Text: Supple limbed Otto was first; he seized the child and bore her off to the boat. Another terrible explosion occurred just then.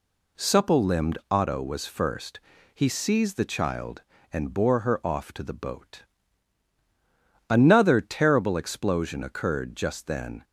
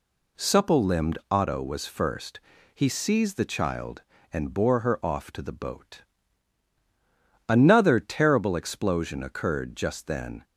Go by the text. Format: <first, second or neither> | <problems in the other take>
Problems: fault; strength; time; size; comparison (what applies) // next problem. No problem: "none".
neither | none